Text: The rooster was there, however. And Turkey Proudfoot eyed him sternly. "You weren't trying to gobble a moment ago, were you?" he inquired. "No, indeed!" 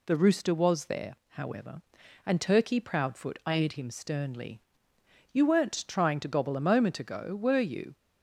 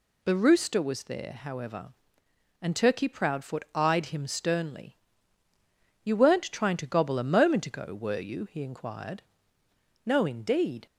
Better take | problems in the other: second | stops before "he inquired No indeed"; at 7.9 s

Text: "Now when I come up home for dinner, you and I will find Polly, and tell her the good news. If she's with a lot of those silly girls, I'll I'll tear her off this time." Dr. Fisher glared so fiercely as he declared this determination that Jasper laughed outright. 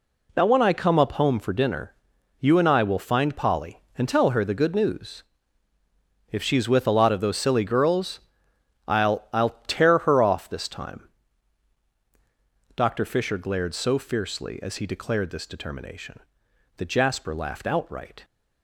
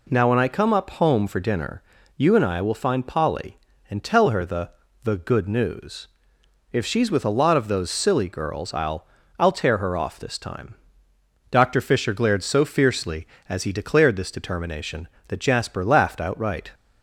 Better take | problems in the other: first | says "the" twice; at 5.0 s // pauses between "I'll" and "I'll"; slight; at 9.0 s; 0.32 s long

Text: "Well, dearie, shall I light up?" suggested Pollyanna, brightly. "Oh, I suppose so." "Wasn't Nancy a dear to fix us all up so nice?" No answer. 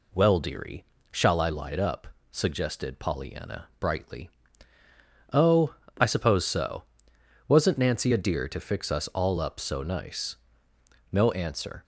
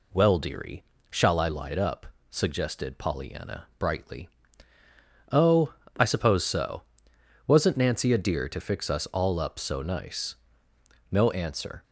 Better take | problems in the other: neither | none

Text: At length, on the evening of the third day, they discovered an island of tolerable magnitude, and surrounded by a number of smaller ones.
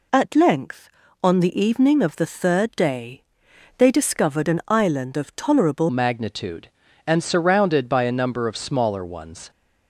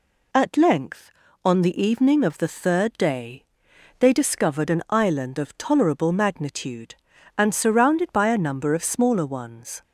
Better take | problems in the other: second | changes voice at "magnitude"; from 5.8 s on; 3.6 s long

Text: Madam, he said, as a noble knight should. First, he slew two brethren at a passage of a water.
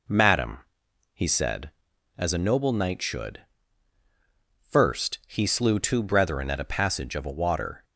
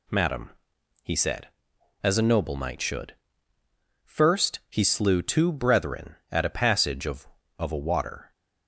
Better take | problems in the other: first | says "of" twice; at 7.5 s

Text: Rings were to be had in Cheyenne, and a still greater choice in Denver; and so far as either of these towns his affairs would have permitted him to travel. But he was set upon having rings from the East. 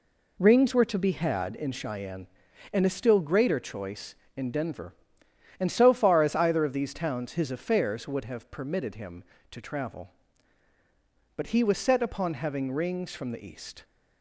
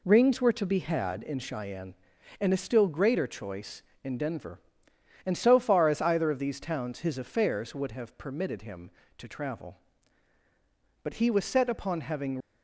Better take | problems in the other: first | stops before "rings from the East"; at 12.4 s

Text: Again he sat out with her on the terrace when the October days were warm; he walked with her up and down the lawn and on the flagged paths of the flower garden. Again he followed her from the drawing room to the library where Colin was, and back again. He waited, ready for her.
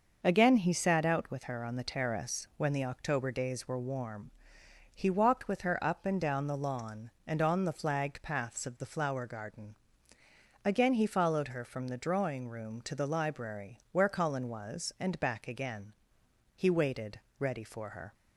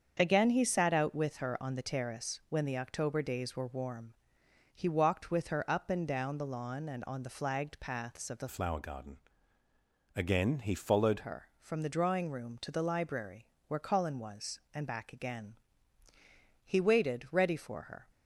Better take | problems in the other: first | starts louder than the rest; strong; until 1.2 s; 7 dB; noticeable in the first // changes voice from "flower" to "followed"; from 8.4 to 11.1 s; 2.7 s long // pauses between "library" and "where"; slight; at 13.4 s; 0.20 s long

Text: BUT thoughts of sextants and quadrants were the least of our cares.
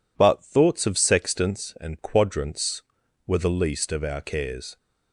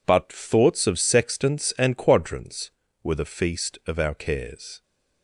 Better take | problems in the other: first | says "feast" for "least"; at 3.2 s

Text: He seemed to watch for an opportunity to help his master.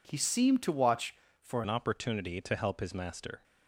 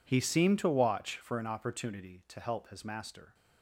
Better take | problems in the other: second | changes voice at "an"; from 1.6 s on; 1.8 s long

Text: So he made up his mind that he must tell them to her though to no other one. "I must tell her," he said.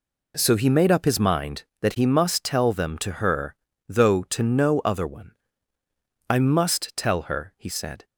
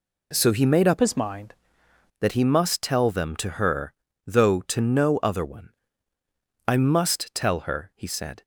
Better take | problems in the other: first | changes voice from "his" to "mind"; from 0.9 to 1.5 s; 0.6 s long // pauses between "her" and "though"; slight; at 3.9 s; 0.34 s long; slight in the first

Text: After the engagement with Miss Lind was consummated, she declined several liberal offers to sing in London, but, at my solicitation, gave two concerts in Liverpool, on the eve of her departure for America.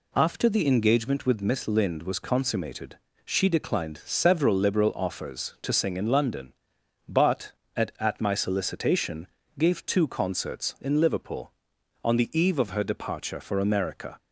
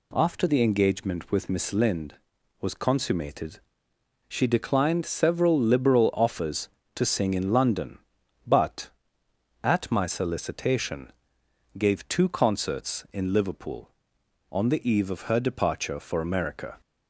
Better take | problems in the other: second | says "at" twice; at 7.9 s

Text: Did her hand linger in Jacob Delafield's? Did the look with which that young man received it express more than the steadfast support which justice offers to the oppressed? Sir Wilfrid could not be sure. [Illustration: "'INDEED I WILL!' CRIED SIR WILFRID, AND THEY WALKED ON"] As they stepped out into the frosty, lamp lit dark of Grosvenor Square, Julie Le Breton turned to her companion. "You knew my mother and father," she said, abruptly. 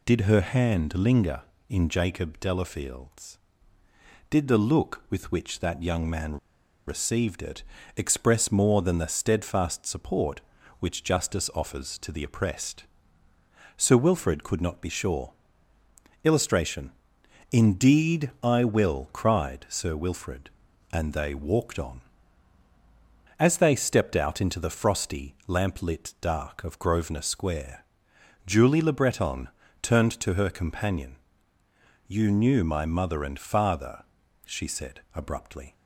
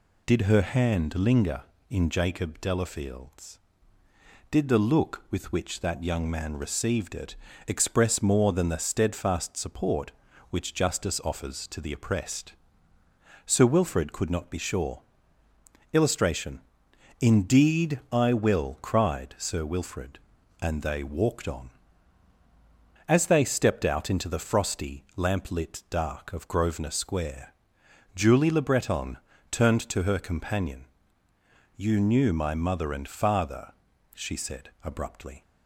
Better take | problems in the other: second | pauses between "man" and "received"; noticeable; at 6.3 s; 0.50 s long // pauses between "it" and "express"; slight; at 7.6 s; 0.34 s long; slight in the second // pauses between "Breton" and "turned"; slight; at 29.4 s; 0.32 s long; slight in the second

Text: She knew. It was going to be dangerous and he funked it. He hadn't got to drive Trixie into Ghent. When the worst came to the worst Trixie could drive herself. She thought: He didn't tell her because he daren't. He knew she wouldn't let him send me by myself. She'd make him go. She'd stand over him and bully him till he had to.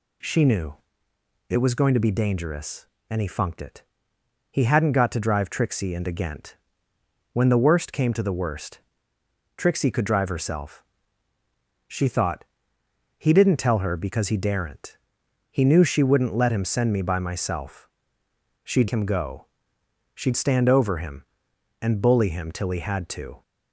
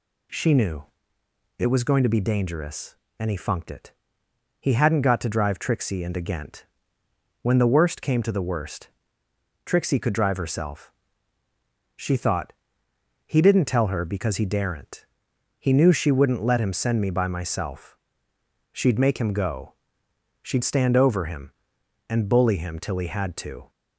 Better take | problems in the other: second | pauses between "worst" and "Trixie"; noticeable; at 8.7 s; 0.78 s long; noticeable in the second // skips "make"; at 18.8 s

